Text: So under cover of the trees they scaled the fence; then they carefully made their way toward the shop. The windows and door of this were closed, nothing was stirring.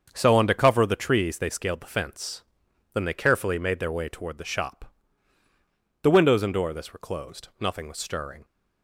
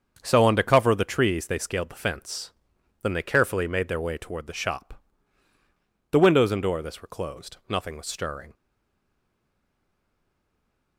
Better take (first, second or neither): first